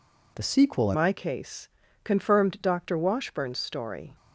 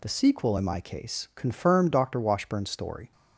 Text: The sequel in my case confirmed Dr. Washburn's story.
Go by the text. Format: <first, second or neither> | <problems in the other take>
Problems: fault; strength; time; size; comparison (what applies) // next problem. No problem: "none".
second | changes voice at "my"; from 0.9 s on; 3.2 s long // pauses between "case" and "confirmed"; slight; at 1.6 s; 0.36 s long